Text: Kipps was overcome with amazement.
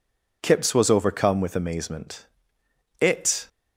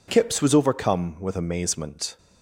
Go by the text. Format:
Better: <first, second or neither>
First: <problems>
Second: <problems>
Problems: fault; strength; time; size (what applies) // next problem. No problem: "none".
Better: second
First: goes on to say "It"; slight; from 2.9 s on; 0.48 s long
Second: none